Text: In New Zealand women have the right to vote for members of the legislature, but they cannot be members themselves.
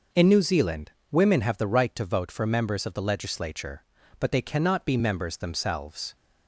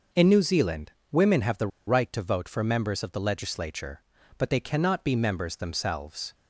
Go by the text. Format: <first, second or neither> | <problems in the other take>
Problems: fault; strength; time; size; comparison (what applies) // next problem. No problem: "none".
first | pauses between "Zealand" and "women"; slight; at 0.9 s; 0.18 s long; slight in the first // pauses between "the" and "right"; slight; at 1.7 s; 0.18 s long